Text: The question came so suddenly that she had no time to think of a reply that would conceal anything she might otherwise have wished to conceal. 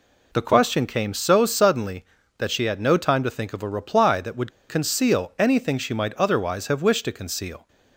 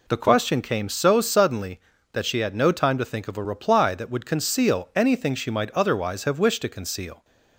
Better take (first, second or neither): second